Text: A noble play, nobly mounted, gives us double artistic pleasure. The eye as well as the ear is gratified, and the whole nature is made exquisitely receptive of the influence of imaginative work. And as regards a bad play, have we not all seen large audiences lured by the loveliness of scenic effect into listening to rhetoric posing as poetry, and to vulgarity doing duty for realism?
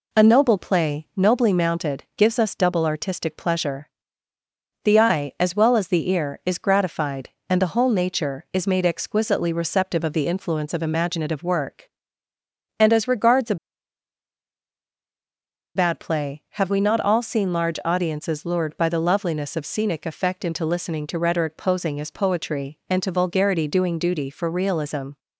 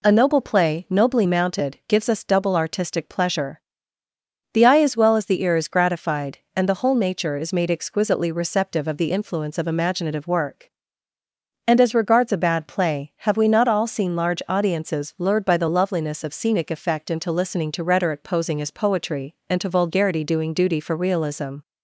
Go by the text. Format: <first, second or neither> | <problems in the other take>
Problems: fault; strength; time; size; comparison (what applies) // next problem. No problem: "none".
second | pauses between "a" and "bad"; strong; at 13.5 s; 2.2 s long